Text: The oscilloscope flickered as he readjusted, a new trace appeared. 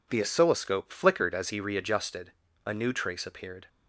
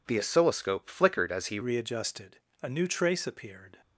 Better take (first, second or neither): first